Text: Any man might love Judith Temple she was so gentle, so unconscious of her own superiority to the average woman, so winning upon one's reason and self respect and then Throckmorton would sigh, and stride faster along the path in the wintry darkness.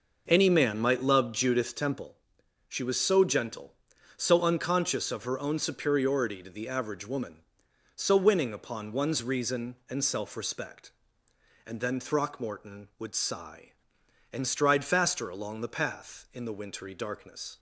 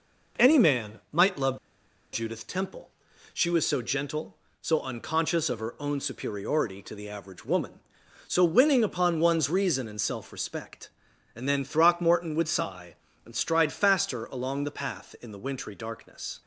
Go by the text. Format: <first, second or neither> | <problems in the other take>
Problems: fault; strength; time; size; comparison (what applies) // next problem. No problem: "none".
first | pauses between "love" and "Judith"; noticeable; at 1.5 s; 0.56 s long // pauses between "Temple" and "she"; at 2.8 s; 0.44 s long; noticeable in the first